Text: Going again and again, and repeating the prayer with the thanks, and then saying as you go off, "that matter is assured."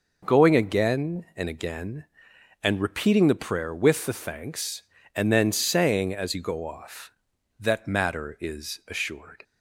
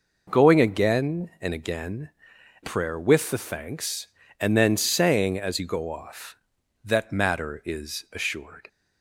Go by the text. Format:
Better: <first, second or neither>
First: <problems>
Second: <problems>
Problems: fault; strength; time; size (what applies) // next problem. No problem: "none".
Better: first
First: none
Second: skips "and repeating the"; at 2.3 s